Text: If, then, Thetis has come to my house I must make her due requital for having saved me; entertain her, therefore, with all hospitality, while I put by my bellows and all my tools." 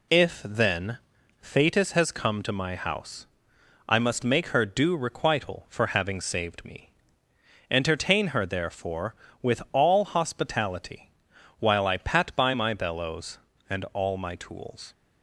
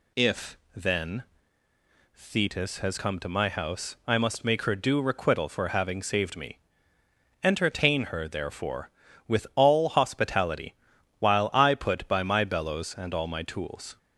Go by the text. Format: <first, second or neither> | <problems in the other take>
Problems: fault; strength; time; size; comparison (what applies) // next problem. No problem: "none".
second | pauses between "house" and "I"; noticeable; at 3.2 s; 0.62 s long // says "pat" for "put"; at 11.9 s